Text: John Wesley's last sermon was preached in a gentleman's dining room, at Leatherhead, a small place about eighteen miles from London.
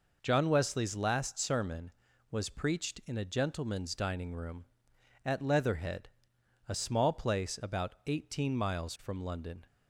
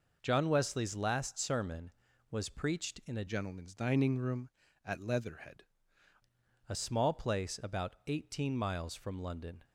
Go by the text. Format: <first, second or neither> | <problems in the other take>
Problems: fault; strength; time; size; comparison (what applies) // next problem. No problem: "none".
first | changes voice from "gentleman's" to "Leatherhead"; from 3.2 to 5.6 s; 2.4 s long